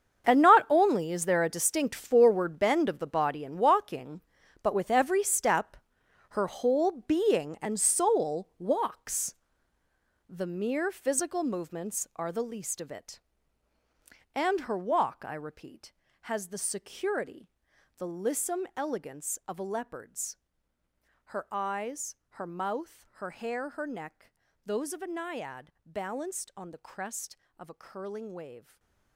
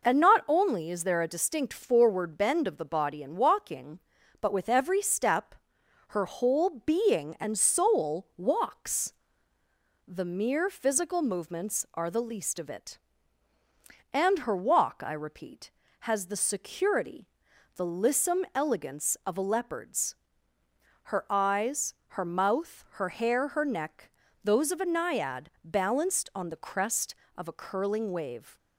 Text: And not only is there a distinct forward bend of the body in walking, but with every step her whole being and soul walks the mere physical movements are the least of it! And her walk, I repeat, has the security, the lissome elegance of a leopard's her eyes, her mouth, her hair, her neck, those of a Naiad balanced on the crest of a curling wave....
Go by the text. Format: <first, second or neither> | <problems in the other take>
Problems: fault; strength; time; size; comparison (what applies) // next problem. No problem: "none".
second | gets quieter; strong; throughout; 14 dB // pauses between "step" and "her"; noticeable; at 5.7 s; 0.52 s long; noticeable in the second // pauses between "walks" and "the"; noticeable; at 9.3 s; 0.92 s long; noticeable in the second // pauses between "leopard's" and "her"; noticeable; at 20.3 s; 0.92 s long; noticeable in the second // stays silent after the last word; slight; from 28.5 s on; 0.6 s long